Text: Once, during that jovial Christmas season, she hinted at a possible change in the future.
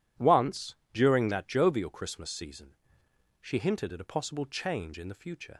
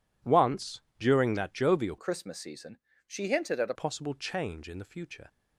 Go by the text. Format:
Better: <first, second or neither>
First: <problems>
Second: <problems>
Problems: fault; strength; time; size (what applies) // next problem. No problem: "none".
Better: first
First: none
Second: changes voice from "Christmas" to "a"; from 1.9 to 3.7 s; 1.8 s long